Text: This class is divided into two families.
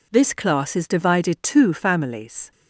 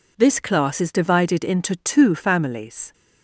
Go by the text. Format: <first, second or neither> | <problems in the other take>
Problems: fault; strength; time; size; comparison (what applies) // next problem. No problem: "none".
second | skips "into"; at 1.3 s